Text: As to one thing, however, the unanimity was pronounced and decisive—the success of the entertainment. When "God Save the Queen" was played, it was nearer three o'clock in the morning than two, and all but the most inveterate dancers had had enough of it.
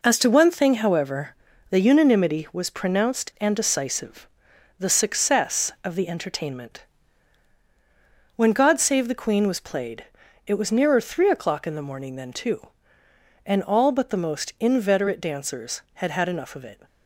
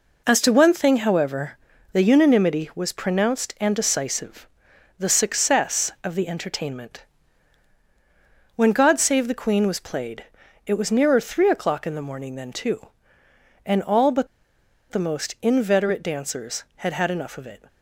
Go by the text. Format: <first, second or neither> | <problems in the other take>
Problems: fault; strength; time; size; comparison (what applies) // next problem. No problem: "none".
first | pauses between "but" and "the"; noticeable; at 14.2 s; 0.65 s long